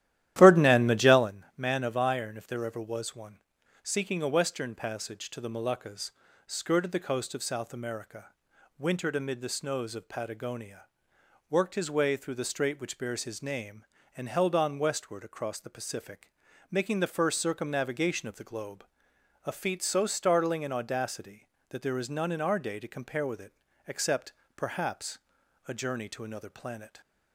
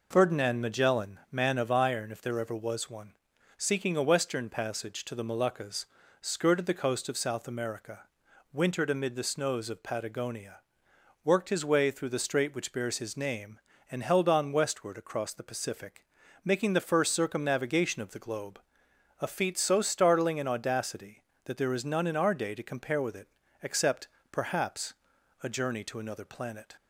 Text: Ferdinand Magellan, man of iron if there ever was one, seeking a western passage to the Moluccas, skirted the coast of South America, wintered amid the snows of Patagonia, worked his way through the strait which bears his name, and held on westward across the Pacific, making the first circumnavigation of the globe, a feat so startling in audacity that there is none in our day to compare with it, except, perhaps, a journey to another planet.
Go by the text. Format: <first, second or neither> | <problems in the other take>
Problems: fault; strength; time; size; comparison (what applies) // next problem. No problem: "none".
second | starts louder than the rest; strong; until 1.3 s; 13 dB